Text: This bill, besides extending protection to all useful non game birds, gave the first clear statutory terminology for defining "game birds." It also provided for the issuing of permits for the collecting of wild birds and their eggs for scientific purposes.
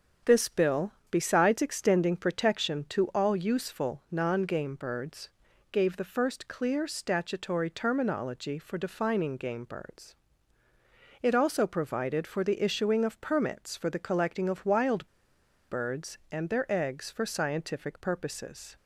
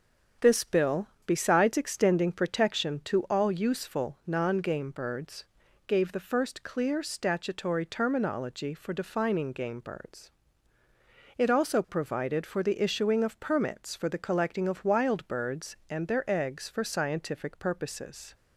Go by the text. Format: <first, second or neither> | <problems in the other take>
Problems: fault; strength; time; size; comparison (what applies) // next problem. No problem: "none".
second | starts louder than the rest; strong; until 1.4 s; 7 dB; strong in the second // pauses between "wild" and "birds"; noticeable; at 15.0 s; 0.60 s long